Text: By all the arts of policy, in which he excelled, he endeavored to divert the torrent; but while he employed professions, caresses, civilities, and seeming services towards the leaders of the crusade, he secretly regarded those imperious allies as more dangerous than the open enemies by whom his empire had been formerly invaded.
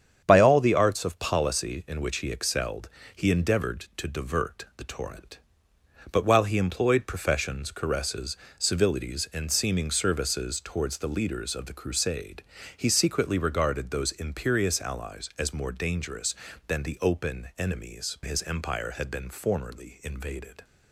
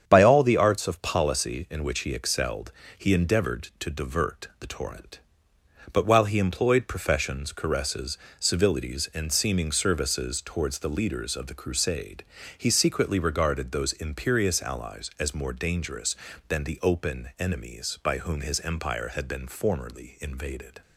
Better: second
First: starts louder than the rest; strong; until 1.2 s; 8 dB // skips "by whom"; at 18.2 s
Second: starts louder than the rest; strong; until 1.0 s; 8 dB

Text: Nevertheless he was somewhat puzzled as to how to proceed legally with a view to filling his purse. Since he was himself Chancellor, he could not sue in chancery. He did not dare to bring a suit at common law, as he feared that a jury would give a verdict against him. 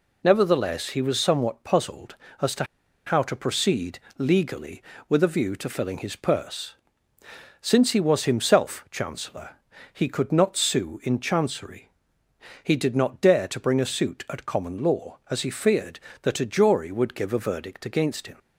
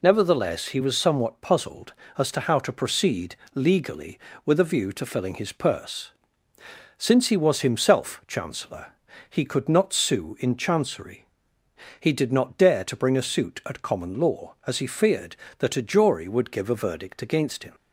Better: second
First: pauses between "to" and "how"; at 2.6 s; 0.42 s long // pauses between "proceed" and "legally"; slight; at 4.0 s; 0.18 s long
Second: pauses between "proceed" and "legally"; slight; at 3.3 s; 0.18 s long

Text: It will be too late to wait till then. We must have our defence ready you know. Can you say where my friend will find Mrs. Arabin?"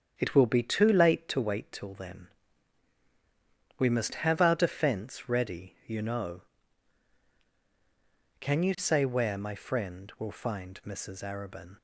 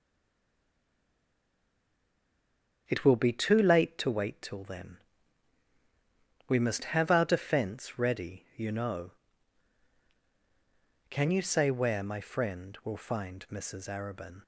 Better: first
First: starts louder than the rest; strong; until 1.1 s; 8 dB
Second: stays silent before the first word; strong; until 2.8 s; 2.8 s long // starts louder than the rest; strong; until 3.8 s; 8 dB

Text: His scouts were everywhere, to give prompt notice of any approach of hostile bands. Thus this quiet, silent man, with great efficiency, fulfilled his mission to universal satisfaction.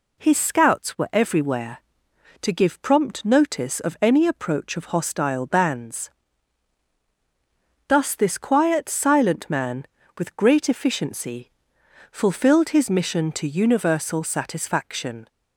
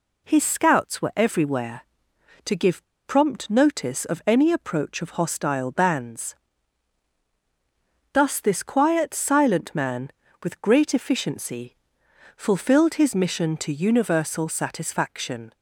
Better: first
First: none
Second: pauses between "give" and "prompt"; slight; at 2.8 s; 0.23 s long

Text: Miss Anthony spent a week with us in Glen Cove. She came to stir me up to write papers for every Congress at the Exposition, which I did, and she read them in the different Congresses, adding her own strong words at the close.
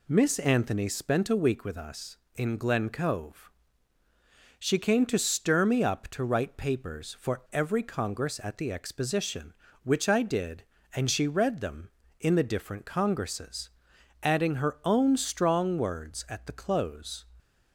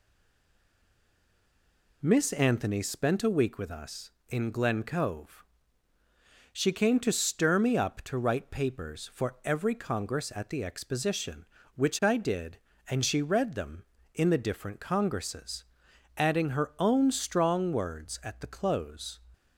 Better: first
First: none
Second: stays silent before the first word; noticeable; until 2.0 s; 2.0 s long

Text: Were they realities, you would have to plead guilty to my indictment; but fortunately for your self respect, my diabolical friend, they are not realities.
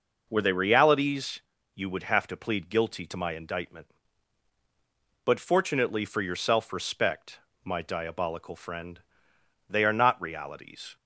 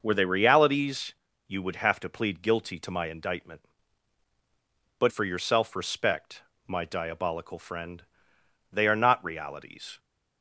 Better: first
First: none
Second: skips "fortunately"; at 5.0 s

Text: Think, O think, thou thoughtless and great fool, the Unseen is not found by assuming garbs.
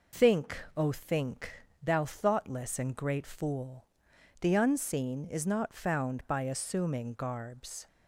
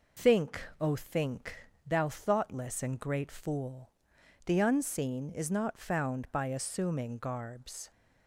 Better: neither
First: none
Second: none

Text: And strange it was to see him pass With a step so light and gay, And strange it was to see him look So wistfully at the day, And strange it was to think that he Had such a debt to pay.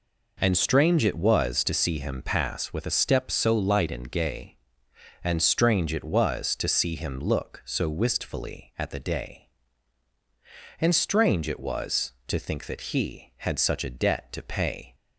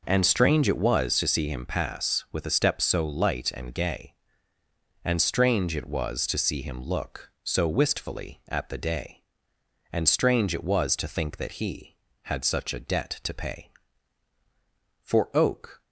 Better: first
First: none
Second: goes on to say "For oak"; noticeable; from 15.0 s on; 0.80 s long

